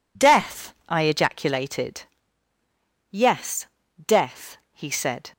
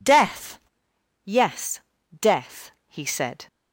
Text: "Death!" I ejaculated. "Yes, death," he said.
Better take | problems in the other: first | skips "I ejaculated"; at 0.9 s

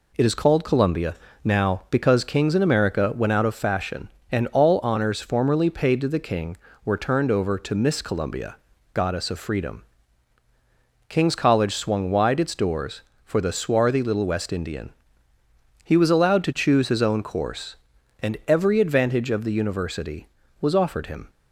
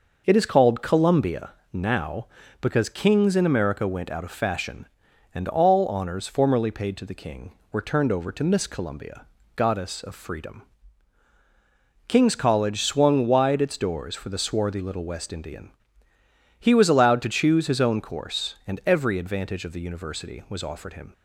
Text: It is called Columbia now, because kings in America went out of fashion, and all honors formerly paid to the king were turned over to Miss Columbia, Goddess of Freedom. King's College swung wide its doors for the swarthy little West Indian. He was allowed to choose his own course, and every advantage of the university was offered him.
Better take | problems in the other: neither | pauses between "Columbia" and "now"; slight; the same in both

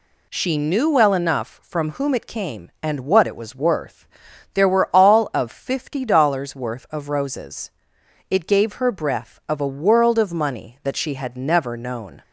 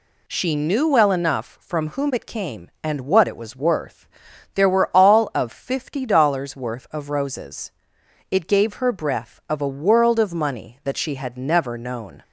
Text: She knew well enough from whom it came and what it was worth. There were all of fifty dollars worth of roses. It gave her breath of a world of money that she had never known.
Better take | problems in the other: neither | none

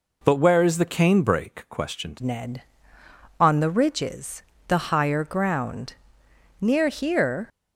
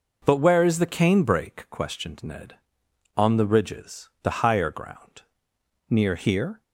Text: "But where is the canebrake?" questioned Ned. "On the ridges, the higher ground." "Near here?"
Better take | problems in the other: second | changes voice at "Ned"; from 2.2 s on; 5.2 s long

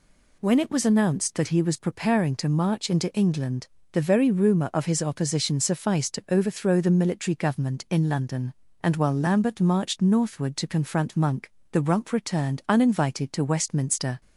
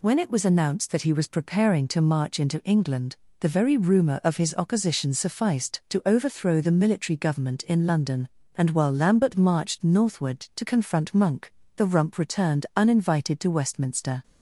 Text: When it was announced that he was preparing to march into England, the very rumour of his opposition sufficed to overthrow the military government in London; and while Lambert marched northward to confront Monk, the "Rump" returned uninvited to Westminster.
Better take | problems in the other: neither | none

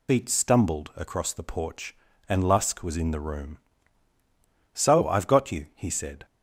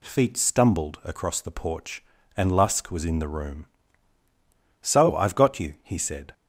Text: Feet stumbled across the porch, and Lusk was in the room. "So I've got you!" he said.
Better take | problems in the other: second | loses the start of "Feet"; at 0.0 s; 135 ms

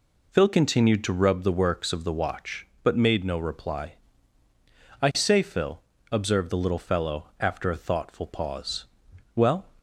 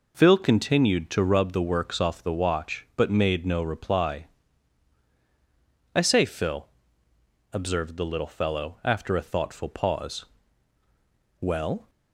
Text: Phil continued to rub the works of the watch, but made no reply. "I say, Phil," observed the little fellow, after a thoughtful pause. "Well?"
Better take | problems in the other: first | says "off" for "of"; at 1.9 s

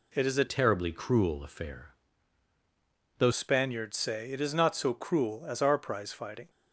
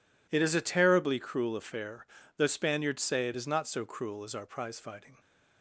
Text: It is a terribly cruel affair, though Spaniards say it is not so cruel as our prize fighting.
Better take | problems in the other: second | changes voice from "terribly" to "though"; from 0.4 to 3.3 s; 2.9 s long

